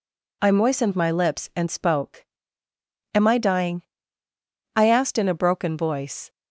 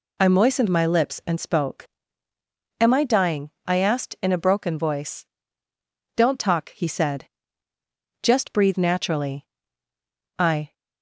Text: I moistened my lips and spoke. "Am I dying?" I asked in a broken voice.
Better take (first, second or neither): first